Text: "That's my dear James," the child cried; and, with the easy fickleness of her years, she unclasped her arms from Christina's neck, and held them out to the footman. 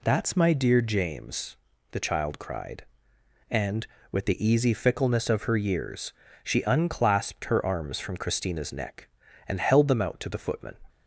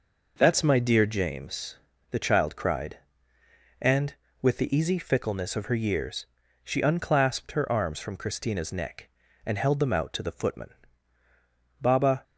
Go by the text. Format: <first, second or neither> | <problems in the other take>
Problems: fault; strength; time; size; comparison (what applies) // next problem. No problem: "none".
first | goes on to say "Baba"; slight; from 11.8 s on; 0.42 s long